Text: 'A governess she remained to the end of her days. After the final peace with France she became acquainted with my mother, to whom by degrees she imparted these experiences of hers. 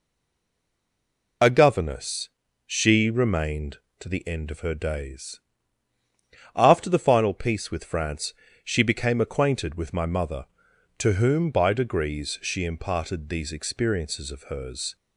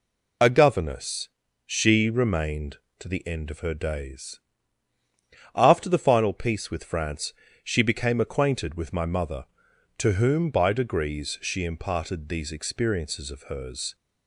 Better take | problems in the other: second | stays silent before the first word; noticeable; until 1.4 s; 1.4 s long // pauses between "governess" and "she"; slight; at 2.2 s; 0.36 s long; slight in the second // pauses between "France" and "she"; slight; at 8.3 s; 0.30 s long; slight in the second

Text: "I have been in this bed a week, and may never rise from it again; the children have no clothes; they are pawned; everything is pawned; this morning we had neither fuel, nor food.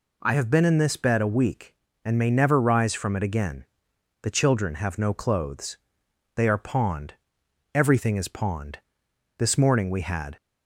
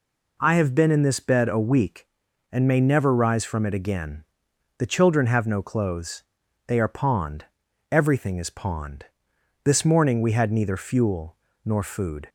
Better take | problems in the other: second | stops before "neither fuel nor food"; at 10.3 s

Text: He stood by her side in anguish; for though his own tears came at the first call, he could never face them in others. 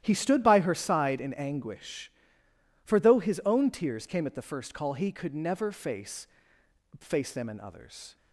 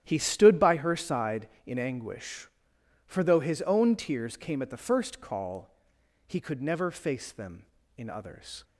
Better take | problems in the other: second | starts louder than the rest; strong; until 1.0 s; 11.5 dB; strong in the second // says "face" twice; at 6.9 s

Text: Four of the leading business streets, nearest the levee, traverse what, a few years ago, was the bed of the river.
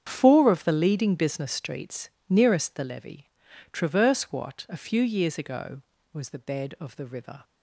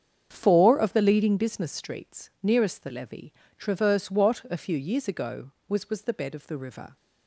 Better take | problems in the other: first | starts louder than the rest; strong; until 1.3 s; 7.5 dB; strong in the first // says "was" twice; at 5.8 s

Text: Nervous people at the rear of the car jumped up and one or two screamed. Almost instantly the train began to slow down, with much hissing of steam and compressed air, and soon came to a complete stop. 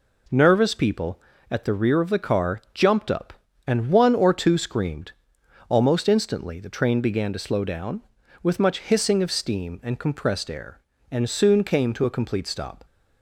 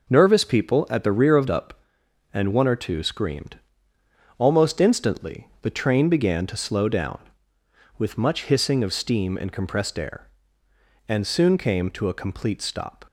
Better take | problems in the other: first | skips "the car jumped"; at 1.4 s // pauses between "instantly" and "the"; slight; at 5.4 s; 0.16 s long

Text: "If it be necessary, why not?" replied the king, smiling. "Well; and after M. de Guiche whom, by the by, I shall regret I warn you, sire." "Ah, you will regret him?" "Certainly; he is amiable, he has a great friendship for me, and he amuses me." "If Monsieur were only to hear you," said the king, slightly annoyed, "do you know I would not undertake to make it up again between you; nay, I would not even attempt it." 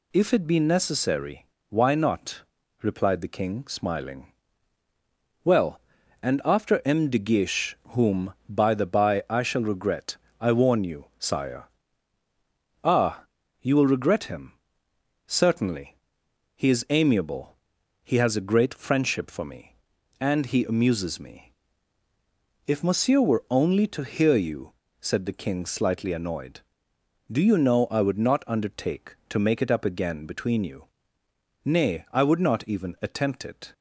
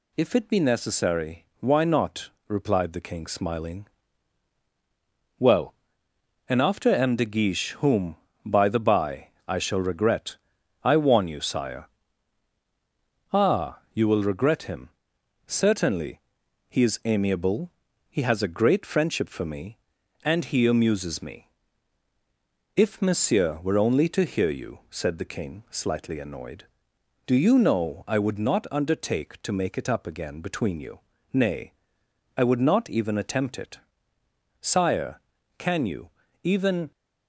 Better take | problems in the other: first | pauses between "regret" and "I"; noticeable; at 10.3 s; 0.48 s long; slight in the first // goes on to say "Sire can you even"; strong; from 34.7 s on; 2.1 s long

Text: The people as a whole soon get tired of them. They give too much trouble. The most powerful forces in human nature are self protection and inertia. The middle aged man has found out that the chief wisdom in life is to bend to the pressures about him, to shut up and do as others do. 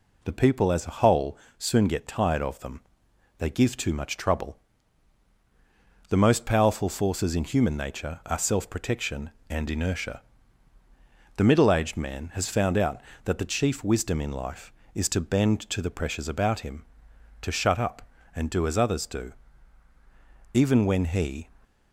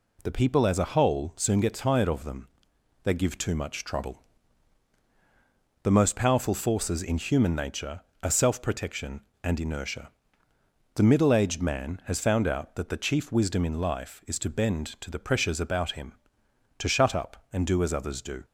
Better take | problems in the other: second | pauses between "whole" and "soon"; slight; at 1.3 s; 0.20 s long // goes on to say "Even when he"; noticeable; from 20.5 s on; 0.98 s long

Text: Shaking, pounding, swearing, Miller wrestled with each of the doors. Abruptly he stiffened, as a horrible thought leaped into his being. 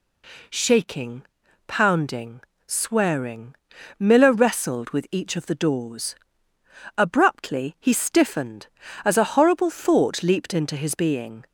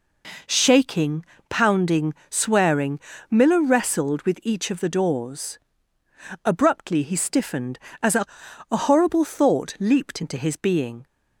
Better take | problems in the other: first | says "a" twice; at 8.7 s

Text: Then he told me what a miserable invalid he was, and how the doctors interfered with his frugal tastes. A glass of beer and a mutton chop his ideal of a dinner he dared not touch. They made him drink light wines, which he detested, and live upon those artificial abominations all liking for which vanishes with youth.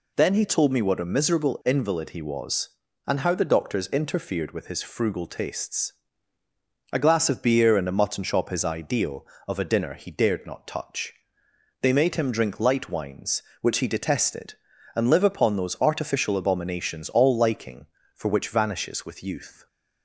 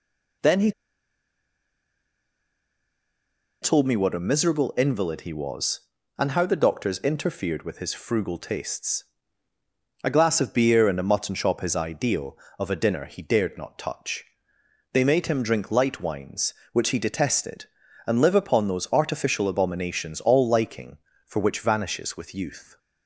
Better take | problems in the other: first | pauses between "he" and "told"; strong; at 0.7 s; 2.9 s long

